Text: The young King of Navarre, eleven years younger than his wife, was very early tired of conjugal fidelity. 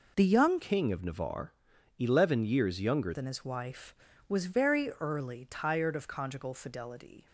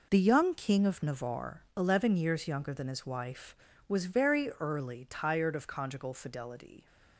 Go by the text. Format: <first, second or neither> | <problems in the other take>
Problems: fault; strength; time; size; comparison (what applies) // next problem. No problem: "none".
second | changes voice from "King" to "younger"; from 0.6 to 3.1 s; 2.5 s long